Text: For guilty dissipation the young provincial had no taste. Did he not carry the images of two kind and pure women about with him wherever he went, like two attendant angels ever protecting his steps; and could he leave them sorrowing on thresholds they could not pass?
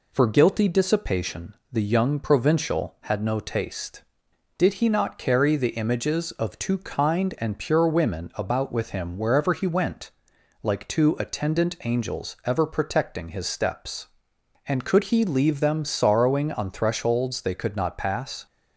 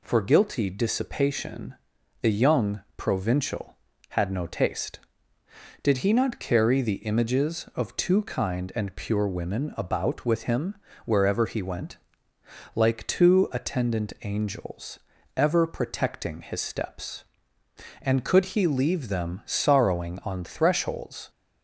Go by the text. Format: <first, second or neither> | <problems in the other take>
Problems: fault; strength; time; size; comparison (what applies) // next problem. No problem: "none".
first | pauses between "dissipation" and "the"; at 1.7 s; 0.44 s long; slight in the first // pauses between "young" and "provincial"; slight; at 2.8 s; 0.16 s long // pauses between "him" and "wherever"; slight; at 10.7 s; 0.30 s long // pauses between "angels" and "ever"; at 14.9 s; 0.38 s long // stops before "they could not pass"; at 21.2 s